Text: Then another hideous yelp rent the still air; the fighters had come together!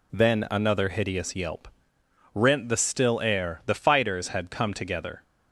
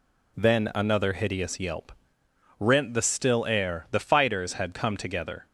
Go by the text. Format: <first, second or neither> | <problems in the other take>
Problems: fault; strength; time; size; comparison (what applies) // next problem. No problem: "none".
neither | pauses between "yelp" and "rent"; noticeable; the same in both